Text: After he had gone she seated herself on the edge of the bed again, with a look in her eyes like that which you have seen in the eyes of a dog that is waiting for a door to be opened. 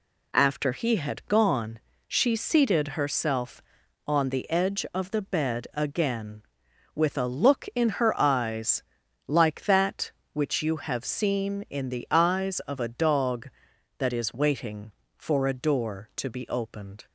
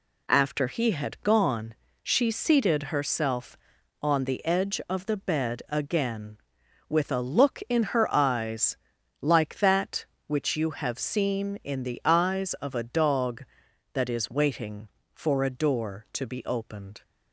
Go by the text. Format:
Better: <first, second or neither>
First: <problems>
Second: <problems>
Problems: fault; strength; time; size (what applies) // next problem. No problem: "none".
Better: neither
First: pauses between "gone" and "she"; slight; at 1.8 s; 0.26 s long // pauses between "eyes" and "like"; at 8.8 s; 0.44 s long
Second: pauses between "gone" and "she"; slight; at 1.7 s; 0.26 s long // pauses between "eyes" and "like"; at 8.7 s; 0.44 s long